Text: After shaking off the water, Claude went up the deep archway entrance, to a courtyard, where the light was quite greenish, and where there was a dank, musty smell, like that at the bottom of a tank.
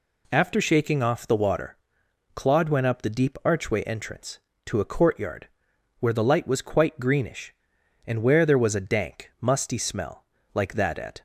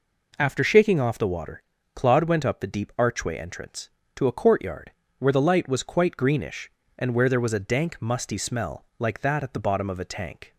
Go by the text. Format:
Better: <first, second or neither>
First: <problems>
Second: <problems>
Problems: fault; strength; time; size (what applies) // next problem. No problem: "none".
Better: second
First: stops before "the bottom of a tank"; at 11.1 s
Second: none